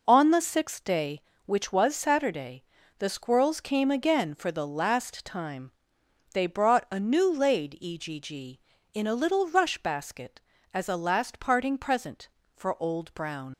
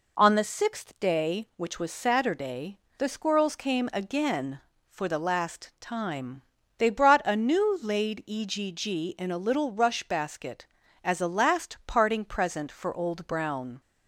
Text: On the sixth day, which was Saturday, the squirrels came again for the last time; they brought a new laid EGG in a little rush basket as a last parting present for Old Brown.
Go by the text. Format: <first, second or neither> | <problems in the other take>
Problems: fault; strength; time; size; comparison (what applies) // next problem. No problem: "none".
second | leaves "Brown" unfinished; at 13.5 s; 95 ms